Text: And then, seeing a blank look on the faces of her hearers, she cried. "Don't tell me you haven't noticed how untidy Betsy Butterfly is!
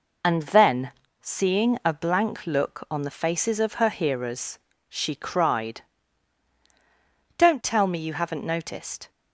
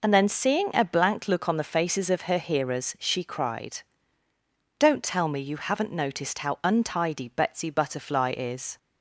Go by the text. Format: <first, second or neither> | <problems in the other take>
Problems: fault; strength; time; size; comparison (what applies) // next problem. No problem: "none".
second | stops before "how untidy Betsy Butterfly is"; at 9.0 s